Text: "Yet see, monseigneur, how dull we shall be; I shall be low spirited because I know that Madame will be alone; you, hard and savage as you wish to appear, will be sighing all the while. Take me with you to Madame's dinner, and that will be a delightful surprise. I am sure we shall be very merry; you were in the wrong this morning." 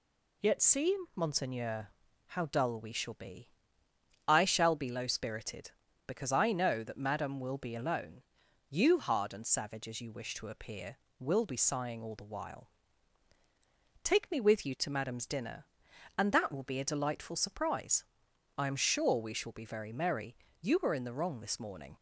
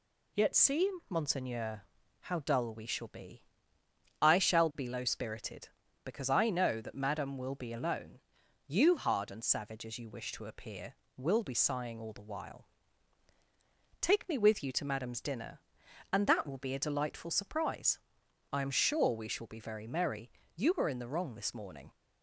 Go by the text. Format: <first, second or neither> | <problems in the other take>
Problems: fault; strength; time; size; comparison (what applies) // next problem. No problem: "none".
neither | none